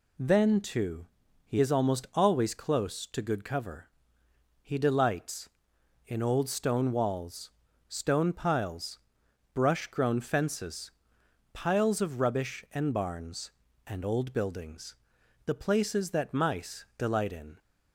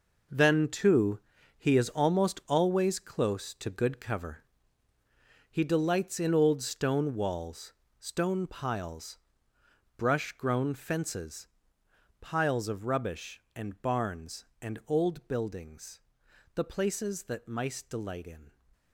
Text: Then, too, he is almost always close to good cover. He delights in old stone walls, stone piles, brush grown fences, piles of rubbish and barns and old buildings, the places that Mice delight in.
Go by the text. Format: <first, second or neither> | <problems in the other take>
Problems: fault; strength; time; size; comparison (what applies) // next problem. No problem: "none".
first | gets quieter; strong; throughout; 10.5 dB